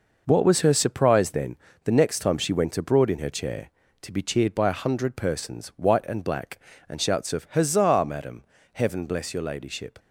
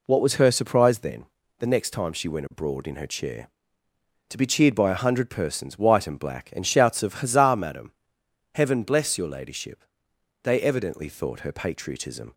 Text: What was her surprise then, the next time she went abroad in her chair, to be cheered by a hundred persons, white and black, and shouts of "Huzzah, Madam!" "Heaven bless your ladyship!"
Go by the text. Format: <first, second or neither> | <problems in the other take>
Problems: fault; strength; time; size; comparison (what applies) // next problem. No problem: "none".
first | goes on to say "They evidently thought her patriotism"; strong; from 10.4 s on; 1.9 s long